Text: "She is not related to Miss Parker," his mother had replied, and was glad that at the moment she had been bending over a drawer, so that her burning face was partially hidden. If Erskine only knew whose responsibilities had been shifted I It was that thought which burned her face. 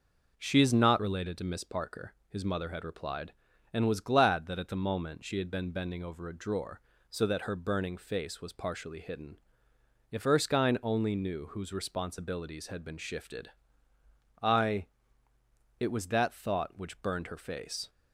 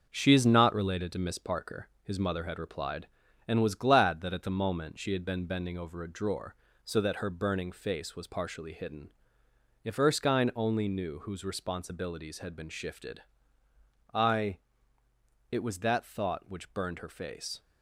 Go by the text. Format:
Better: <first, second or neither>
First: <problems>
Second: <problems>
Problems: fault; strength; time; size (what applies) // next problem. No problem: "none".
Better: first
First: pauses between "shifted" and "I"; noticeable; at 13.4 s; 0.92 s long // pauses between "I" and "It"; noticeable; at 14.8 s; 0.92 s long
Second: gets quieter; noticeable; throughout; 5.5 dB // pauses between "shifted" and "I"; noticeable; at 13.2 s; 0.92 s long // pauses between "I" and "It"; noticeable; at 14.5 s; 0.92 s long